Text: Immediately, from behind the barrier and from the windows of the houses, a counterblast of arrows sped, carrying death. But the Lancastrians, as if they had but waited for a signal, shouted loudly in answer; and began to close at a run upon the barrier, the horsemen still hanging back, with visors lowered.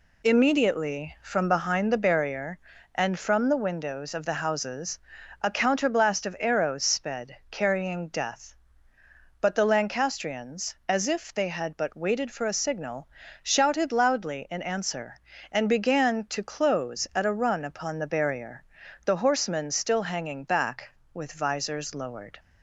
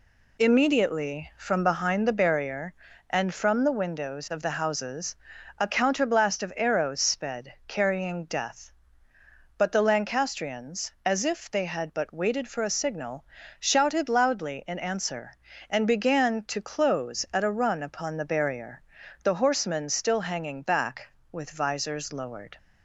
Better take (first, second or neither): neither